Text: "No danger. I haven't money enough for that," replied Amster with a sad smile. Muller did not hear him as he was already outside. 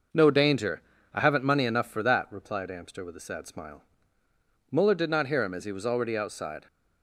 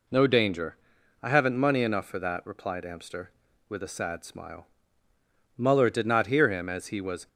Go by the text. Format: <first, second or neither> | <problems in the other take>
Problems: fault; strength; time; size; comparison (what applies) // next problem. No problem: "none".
first | stops before "already outside"; at 7.2 s